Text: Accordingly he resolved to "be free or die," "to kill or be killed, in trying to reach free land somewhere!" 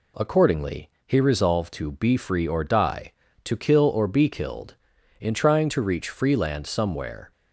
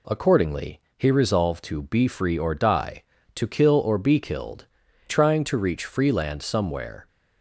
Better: first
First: pauses between "Accordingly" and "he"; slight; at 0.8 s; 0.18 s long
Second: pauses between "Accordingly" and "he"; slight; at 0.7 s; 0.18 s long // skips "in"; at 4.8 s

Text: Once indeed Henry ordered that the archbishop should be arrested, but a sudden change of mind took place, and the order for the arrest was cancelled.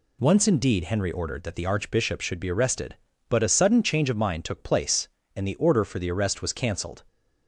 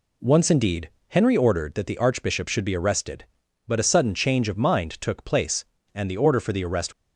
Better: first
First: none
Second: pauses between "indeed" and "Henry"; slight; at 0.8 s; 0.20 s long // stops before "was cancelled"; at 6.9 s

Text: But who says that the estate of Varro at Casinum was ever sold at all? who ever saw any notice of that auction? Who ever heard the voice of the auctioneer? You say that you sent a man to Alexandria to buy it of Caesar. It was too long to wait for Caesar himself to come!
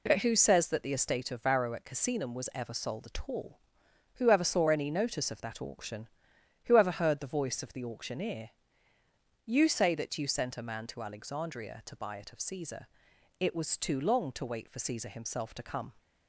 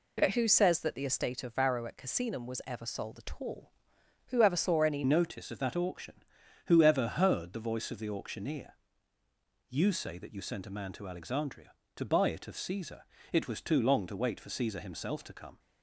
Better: first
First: none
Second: changes voice at "notice"; from 5.0 s on; 10.5 s long

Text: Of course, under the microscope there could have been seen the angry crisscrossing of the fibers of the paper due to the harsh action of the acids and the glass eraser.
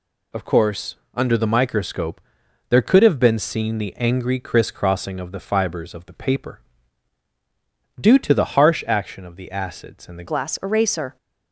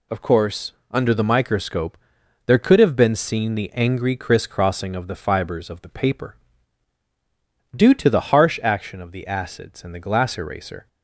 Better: second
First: pauses between "microscope" and "there"; noticeable; at 2.1 s; 0.50 s long // pauses between "paper" and "due"; strong; at 6.6 s; 1.3 s long // changes voice at "glass"; from 10.2 s on; 0.9 s long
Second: pauses between "microscope" and "there"; noticeable; at 1.9 s; 0.50 s long // pauses between "paper" and "due"; strong; at 6.3 s; 1.3 s long

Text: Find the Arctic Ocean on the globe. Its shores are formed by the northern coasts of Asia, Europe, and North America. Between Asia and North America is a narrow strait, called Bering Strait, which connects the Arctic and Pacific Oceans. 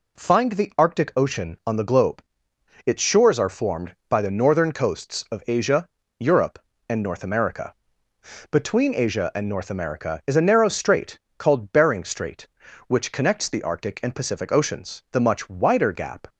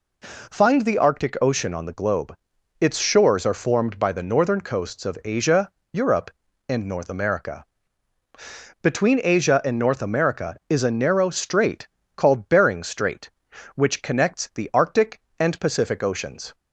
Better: second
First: goes on to say "The much wider gap"; noticeable; from 15.1 s on; 1.1 s long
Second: none

